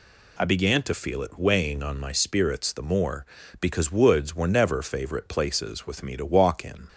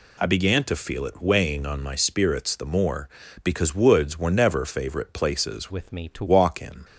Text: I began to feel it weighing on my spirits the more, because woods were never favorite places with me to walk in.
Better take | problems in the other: first | changes voice from "with" to "to"; from 5.7 to 6.2 s; 0.5 s long

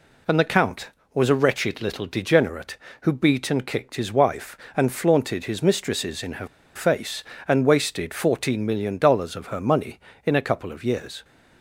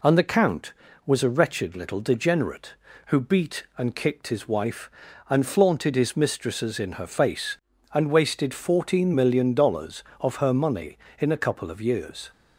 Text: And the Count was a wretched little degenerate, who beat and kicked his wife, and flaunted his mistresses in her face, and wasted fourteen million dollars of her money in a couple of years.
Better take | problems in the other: second | pauses between "her" and "face"; slight; at 6.4 s; 0.28 s long

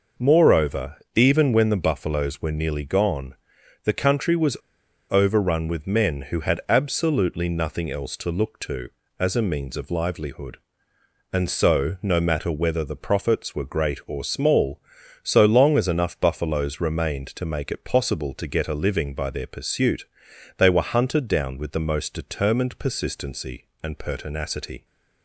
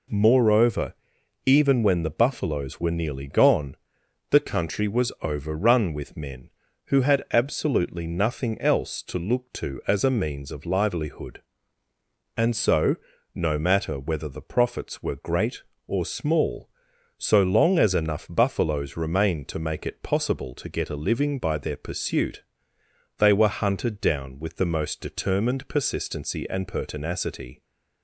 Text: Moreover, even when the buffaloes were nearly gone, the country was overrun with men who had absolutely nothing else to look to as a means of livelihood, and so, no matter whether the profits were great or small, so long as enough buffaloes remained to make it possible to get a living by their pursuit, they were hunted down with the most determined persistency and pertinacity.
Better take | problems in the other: second | pauses between "was" and "overrun"; noticeable; at 4.5 s; 0.54 s long

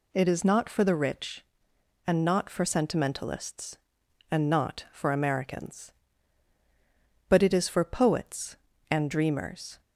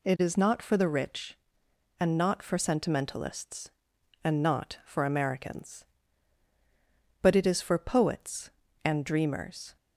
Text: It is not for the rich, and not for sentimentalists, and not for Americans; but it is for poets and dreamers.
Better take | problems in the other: neither | none

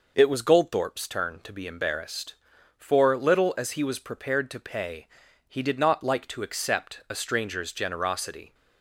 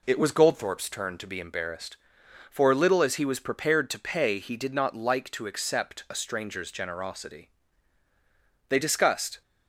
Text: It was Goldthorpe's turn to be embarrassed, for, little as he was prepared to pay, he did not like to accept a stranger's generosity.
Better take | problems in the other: first | goes on to say "They discussed"; noticeable; from 8.6 s on; 0.73 s long

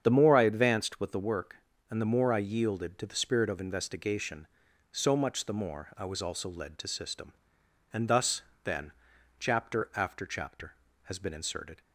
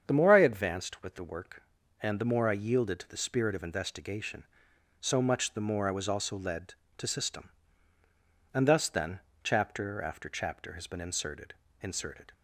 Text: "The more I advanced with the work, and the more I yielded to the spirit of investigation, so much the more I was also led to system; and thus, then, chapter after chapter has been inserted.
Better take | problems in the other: first | starts louder than the rest; strong; until 1.0 s; 7.5 dB; strong in the first // says "inserted" twice; at 11.8 s

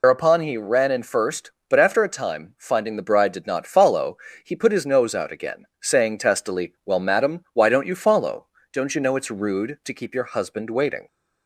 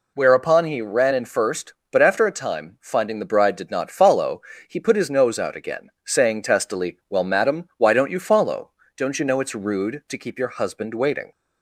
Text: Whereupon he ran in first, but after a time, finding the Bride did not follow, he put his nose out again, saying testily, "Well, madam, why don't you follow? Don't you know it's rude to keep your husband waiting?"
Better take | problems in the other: second | loses the start of "Whereupon"; at 0.0 s; 130 ms

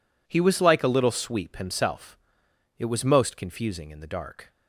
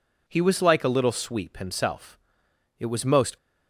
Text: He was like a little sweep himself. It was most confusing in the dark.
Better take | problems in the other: first | stops before "confusing in the dark"; at 3.3 s

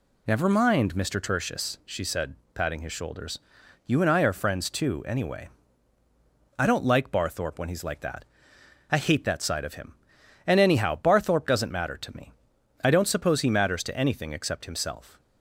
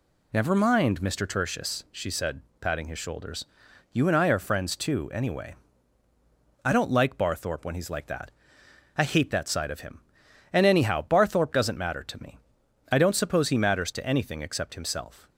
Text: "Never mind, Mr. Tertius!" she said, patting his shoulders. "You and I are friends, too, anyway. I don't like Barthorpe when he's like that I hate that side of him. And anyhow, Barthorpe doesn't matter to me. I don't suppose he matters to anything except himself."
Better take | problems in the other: neither | pauses between "that" and "I"; noticeable; the same in both

